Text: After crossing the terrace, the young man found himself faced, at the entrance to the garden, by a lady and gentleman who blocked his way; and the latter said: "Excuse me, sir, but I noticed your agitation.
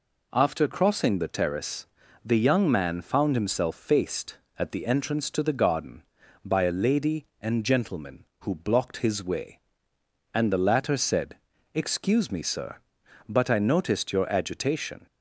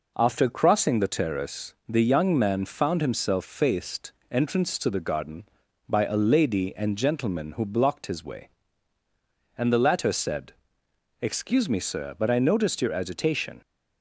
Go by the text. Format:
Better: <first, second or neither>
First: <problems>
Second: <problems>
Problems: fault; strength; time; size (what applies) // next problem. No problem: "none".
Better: first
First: none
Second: skips "at the"; at 4.2 s